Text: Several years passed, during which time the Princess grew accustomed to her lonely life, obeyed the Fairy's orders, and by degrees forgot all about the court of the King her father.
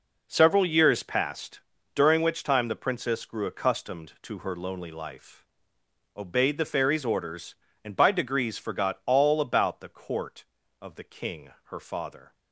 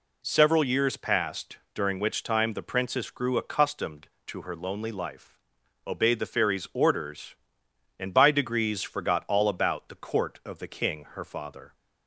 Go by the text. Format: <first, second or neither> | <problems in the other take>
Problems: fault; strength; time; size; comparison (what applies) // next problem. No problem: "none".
neither | none